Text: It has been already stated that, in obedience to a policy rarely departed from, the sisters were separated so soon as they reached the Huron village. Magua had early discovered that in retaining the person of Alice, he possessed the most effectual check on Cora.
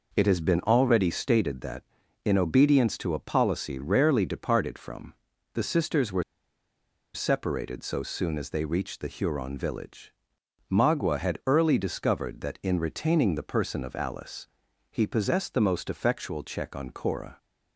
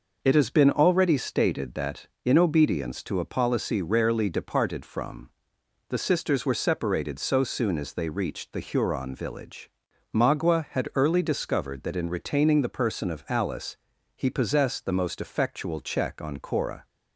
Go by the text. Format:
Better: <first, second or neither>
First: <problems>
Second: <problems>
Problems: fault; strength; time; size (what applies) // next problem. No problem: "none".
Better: second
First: pauses between "were" and "separated"; noticeable; at 6.2 s; 0.91 s long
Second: none